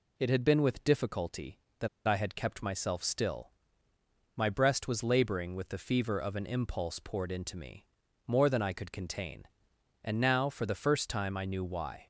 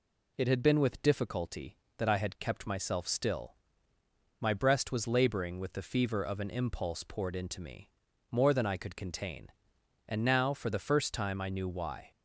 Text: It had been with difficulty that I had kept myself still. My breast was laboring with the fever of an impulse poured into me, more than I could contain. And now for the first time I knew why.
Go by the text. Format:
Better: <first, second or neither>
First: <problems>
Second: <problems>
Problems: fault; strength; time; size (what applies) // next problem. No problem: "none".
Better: second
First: pauses between "that" and "I"; slight; at 1.8 s; 0.20 s long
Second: none